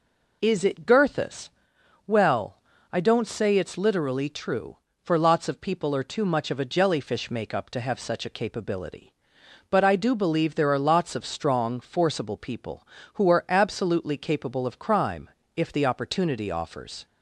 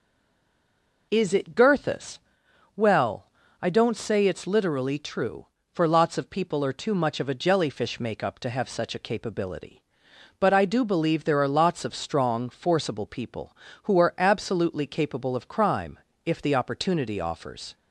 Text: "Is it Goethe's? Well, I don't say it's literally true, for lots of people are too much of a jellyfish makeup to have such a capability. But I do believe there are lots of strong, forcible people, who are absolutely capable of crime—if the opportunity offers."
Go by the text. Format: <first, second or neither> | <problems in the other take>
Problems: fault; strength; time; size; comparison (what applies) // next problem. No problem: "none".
first | stays silent before the first word; until 1.1 s; 1.1 s long